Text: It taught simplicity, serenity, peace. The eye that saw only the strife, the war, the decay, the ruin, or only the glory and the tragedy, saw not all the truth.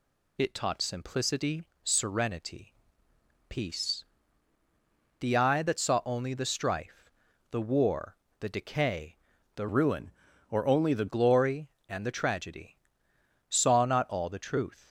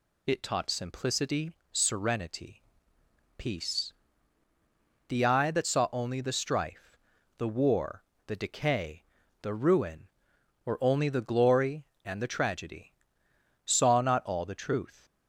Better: second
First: changes voice from "ruin" to "the"; from 9.6 to 11.0 s; 1.4 s long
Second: none

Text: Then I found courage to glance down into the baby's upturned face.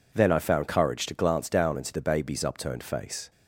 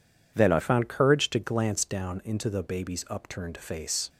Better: first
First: none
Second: changes voice at "found"; from 0.5 s on; 3.5 s long

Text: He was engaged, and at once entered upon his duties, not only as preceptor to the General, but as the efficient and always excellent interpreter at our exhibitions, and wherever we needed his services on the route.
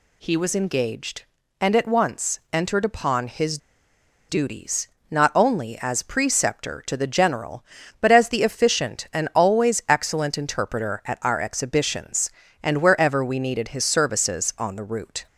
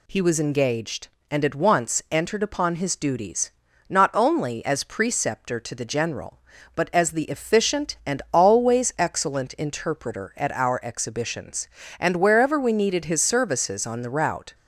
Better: second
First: pauses between "his" and "duties"; noticeable; at 3.5 s; 0.71 s long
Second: none

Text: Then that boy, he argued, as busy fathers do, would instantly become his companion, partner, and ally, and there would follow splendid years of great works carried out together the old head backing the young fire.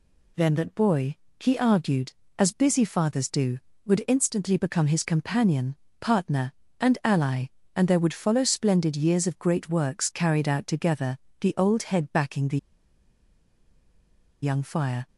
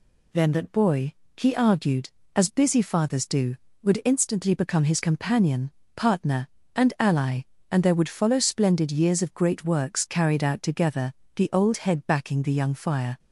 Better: second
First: pauses between "together" and "the"; slight; at 11.1 s; 0.22 s long // pauses between "the" and "young"; strong; at 12.5 s; 1.8 s long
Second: pauses between "together" and "the"; slight; at 11.1 s; 0.22 s long

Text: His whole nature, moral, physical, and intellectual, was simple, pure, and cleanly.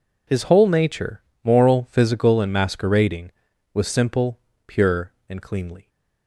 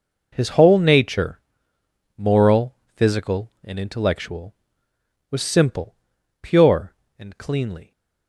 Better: second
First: says "masquerading" for "intellectual"; at 2.5 s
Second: none

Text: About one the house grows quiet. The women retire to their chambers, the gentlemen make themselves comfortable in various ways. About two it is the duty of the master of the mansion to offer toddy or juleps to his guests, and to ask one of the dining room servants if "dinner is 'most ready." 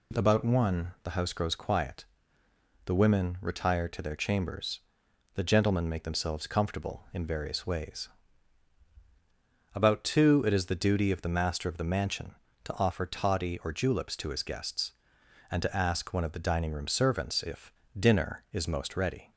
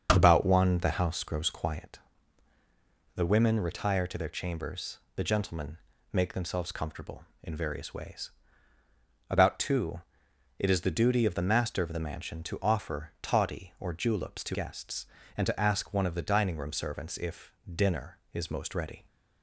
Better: first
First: pauses between "if" and "dinner"; slight; at 17.7 s; 0.24 s long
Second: starts louder than the rest; until 1.1 s; 6.5 dB // pauses between "gentlemen" and "make"; slight; at 5.7 s; 0.34 s long // pauses between "two" and "it"; noticeable; at 10.0 s; 0.58 s long // skips "his"; at 14.5 s // pauses between "if" and "dinner"; slight; at 17.5 s; 0.24 s long

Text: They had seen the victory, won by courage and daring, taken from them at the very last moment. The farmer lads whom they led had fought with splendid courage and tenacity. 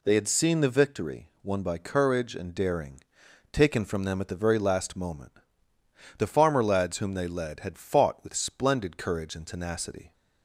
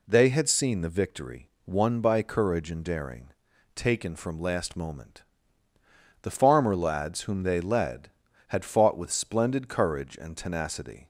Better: first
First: none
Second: skips "them at the very"; at 4.4 s

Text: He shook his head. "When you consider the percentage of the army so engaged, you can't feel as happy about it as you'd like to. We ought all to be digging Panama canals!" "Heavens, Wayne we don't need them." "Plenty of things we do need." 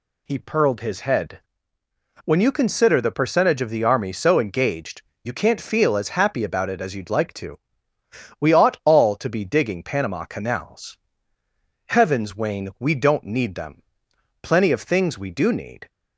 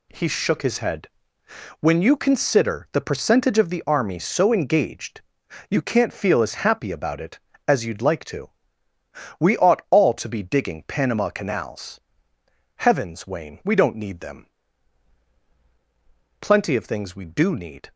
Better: second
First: says "purled" for "shook"; at 0.3 s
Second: none

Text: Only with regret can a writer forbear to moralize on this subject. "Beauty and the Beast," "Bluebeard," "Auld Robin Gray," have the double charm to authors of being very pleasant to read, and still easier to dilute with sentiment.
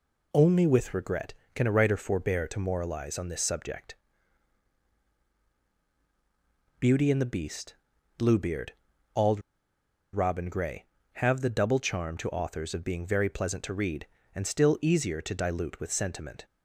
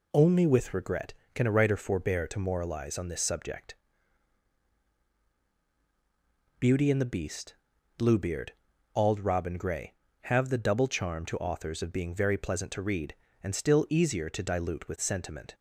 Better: second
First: pauses between "Auld" and "Robin"; noticeable; at 9.3 s; 0.73 s long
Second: none

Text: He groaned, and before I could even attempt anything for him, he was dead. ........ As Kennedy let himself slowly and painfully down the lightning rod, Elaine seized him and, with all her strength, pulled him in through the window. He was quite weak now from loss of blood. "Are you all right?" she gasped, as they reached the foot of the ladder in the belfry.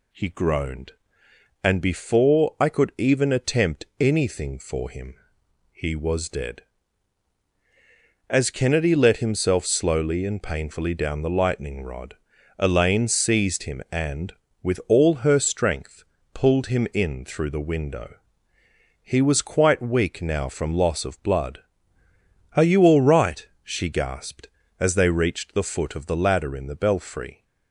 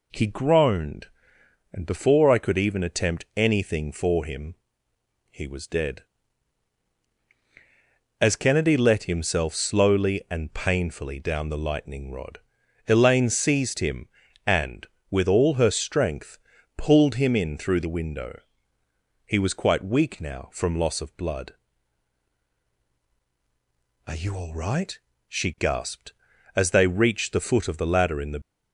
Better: first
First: none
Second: stops before "belfry"; at 28.4 s

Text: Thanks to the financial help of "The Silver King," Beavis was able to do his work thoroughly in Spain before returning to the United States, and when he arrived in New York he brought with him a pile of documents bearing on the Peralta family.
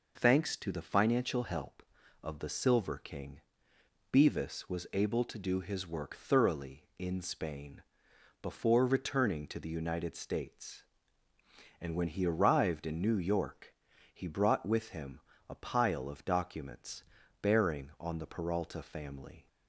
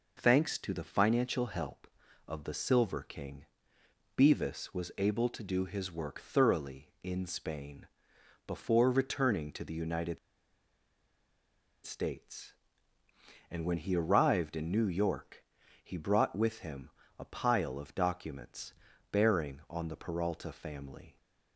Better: first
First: pauses between "Spain" and "before"; noticeable; at 7.8 s; 0.62 s long // pauses between "York" and "he"; at 13.7 s; 0.40 s long // pauses between "him" and "a"; slight; at 15.1 s; 0.30 s long // pauses between "documents" and "bearing"; at 17.0 s; 0.40 s long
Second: pauses between "Spain" and "before"; noticeable; at 7.8 s; 0.62 s long // pauses between "United" and "States"; strong; at 10.1 s; 1.6 s long // pauses between "York" and "he"; at 15.4 s; 0.40 s long // pauses between "him" and "a"; slight; at 16.8 s; 0.30 s long // pauses between "documents" and "bearing"; at 18.7 s; 0.40 s long

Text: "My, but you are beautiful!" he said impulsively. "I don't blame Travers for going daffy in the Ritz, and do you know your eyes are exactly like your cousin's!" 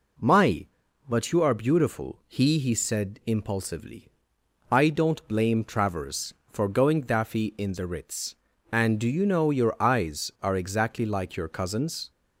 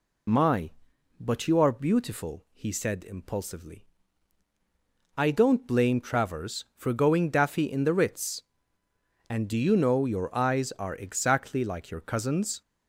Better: second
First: says "he" twice; at 2.5 s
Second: none

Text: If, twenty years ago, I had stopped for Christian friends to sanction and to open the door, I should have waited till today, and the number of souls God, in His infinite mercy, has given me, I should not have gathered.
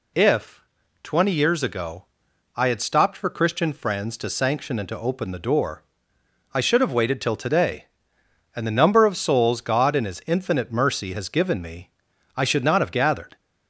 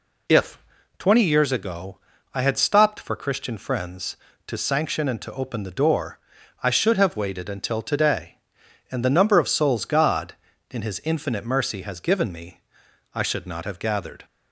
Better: first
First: none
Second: says "until" for "till"; at 7.4 s

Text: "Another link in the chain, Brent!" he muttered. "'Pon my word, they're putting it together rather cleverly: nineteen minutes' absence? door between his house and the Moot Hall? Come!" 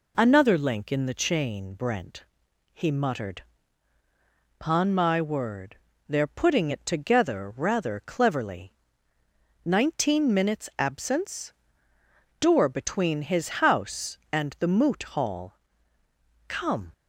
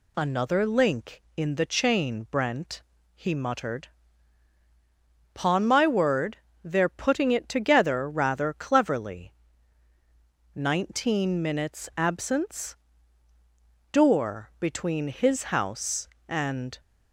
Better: first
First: none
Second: stops before "the Moot Hall Come"; at 16.7 s

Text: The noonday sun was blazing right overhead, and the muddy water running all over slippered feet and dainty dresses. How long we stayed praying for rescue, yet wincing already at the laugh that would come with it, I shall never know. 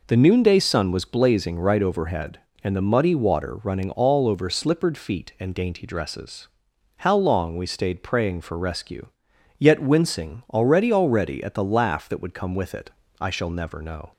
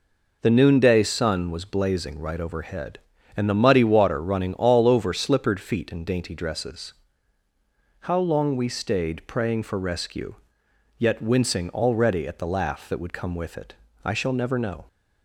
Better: second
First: says "already" twice; at 10.9 s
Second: none

